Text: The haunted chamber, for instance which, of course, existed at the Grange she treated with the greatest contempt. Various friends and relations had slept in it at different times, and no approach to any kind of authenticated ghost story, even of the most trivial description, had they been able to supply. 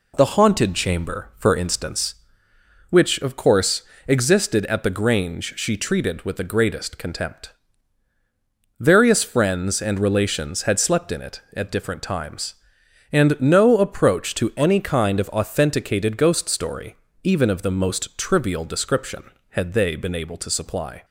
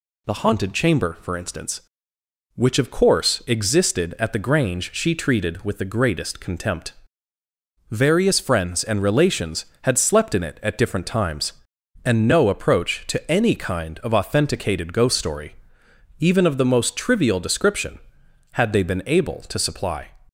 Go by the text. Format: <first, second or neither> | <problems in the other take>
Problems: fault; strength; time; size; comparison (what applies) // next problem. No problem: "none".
neither | none